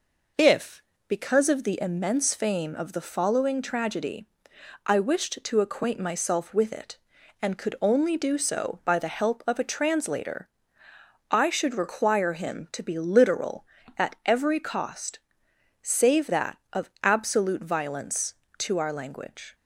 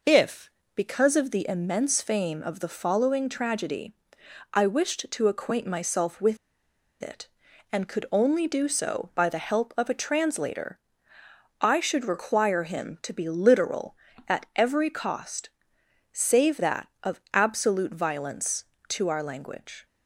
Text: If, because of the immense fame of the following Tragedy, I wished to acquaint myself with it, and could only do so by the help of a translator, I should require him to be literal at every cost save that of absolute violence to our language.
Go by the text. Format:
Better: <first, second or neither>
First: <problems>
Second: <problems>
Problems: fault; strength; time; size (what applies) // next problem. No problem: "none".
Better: first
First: pauses between "cost" and "save"; noticeable; at 15.1 s; 0.68 s long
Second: pauses between "with" and "it"; noticeable; at 6.3 s; 0.65 s long // pauses between "cost" and "save"; noticeable; at 15.4 s; 0.68 s long